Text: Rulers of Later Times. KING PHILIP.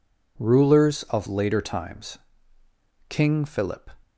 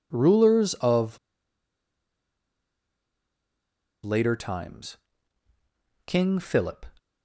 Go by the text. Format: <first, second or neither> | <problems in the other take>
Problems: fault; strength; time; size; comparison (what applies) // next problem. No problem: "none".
first | pauses between "of" and "Later"; strong; at 1.1 s; 2.8 s long